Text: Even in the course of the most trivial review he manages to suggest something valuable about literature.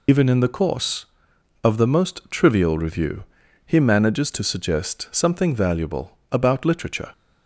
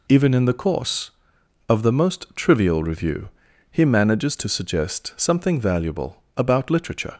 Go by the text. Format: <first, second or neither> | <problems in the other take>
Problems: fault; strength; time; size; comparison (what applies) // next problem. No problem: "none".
second | loses the start of "Even"; at 0.0 s; 45 ms // pauses between "review" and "he"; at 3.2 s; 0.40 s long; also in the second